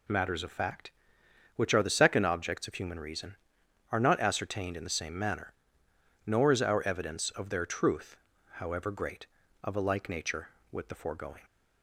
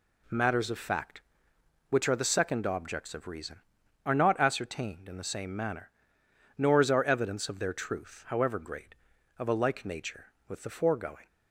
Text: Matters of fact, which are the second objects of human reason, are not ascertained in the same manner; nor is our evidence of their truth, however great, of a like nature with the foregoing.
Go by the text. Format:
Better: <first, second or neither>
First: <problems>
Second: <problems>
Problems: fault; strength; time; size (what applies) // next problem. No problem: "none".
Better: first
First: none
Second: skips "human"; at 3.2 s